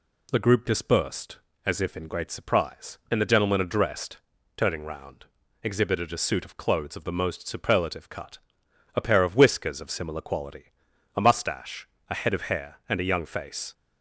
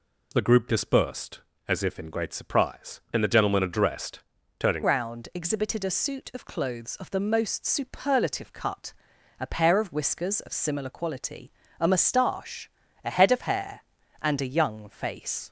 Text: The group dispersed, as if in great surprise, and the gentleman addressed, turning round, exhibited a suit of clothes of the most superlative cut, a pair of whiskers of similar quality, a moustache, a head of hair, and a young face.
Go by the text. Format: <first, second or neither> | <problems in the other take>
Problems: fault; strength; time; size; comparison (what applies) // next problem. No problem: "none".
first | changes voice at "round"; from 4.8 s on; 10.6 s long